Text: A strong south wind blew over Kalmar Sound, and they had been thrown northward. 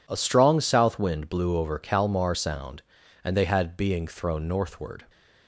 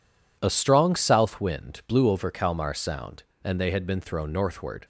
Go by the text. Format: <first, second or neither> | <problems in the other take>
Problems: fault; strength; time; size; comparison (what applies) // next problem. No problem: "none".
second | says "being" for "been"; at 3.7 s